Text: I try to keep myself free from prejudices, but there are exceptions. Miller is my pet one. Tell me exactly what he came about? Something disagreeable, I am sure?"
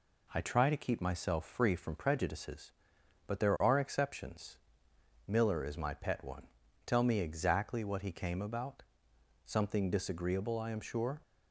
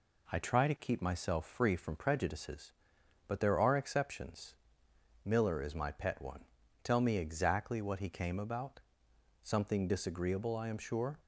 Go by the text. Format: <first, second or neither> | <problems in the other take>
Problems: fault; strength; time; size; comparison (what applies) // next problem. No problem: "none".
neither | none